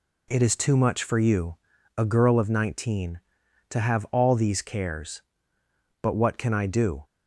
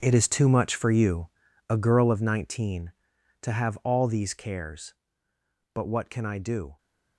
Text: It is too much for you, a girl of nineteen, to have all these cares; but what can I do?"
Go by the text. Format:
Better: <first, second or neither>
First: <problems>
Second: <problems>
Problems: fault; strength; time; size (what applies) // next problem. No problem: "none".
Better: first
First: none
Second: gets quieter; strong; throughout; 13 dB